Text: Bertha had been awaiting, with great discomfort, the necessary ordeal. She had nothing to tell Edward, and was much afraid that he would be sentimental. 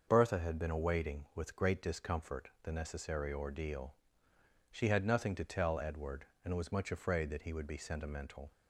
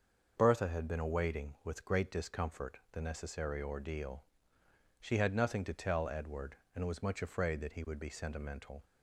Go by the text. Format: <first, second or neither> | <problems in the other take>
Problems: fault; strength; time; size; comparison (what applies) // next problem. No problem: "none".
neither | starts louder than the rest; the same in both